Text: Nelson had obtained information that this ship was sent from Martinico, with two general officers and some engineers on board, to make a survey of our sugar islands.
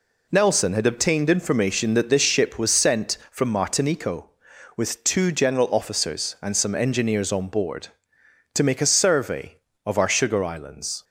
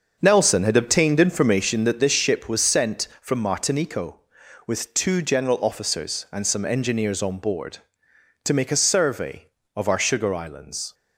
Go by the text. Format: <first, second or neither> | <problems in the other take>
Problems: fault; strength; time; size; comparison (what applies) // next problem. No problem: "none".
first | starts louder than the rest; until 1.9 s; 6.5 dB